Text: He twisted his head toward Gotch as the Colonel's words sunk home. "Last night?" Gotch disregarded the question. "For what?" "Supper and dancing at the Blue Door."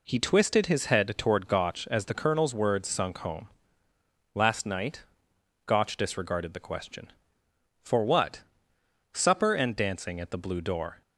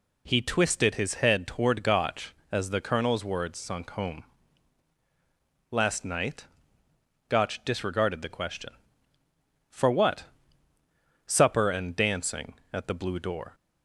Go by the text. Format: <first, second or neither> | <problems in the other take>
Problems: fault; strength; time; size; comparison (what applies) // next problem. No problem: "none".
neither | none